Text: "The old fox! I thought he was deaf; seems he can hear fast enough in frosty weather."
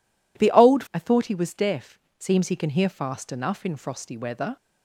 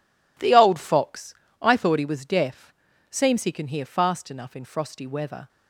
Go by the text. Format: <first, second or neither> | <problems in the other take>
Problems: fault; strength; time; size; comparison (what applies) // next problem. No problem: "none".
second | skips "fox"; at 0.8 s